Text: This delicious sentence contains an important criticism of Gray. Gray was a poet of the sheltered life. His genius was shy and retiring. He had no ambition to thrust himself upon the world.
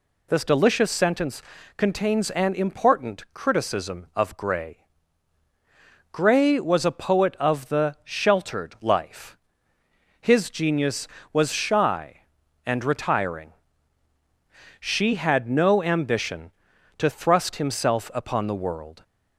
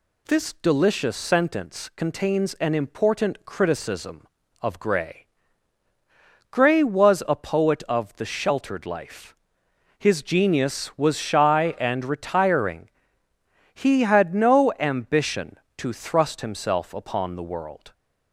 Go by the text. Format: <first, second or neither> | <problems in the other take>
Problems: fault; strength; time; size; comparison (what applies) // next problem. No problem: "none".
second | pauses between "sentence" and "contains"; slight; at 1.4 s; 0.34 s long // says "She" for "He"; at 14.7 s